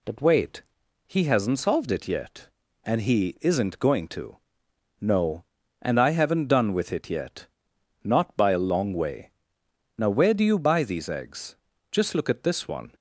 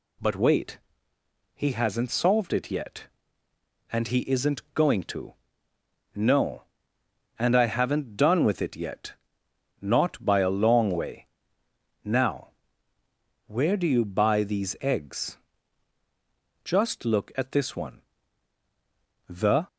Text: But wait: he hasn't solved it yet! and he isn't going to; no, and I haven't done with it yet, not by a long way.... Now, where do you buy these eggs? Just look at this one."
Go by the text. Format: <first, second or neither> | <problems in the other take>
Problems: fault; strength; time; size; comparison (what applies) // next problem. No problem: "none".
first | goes on to say "The"; slight; from 19.2 s on; 0.38 s long